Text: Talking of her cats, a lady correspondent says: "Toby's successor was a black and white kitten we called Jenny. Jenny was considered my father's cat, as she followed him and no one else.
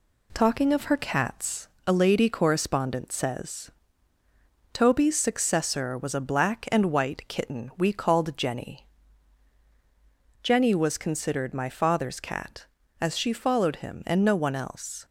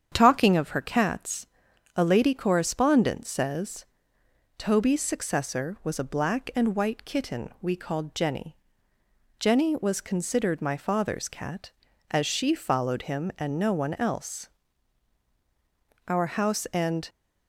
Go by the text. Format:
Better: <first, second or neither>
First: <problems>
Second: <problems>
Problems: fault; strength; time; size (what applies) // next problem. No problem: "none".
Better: first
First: none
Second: starts louder than the rest; strong; until 1.1 s; 8 dB // goes on to say "Our house and"; noticeable; from 16.0 s on; 1.0 s long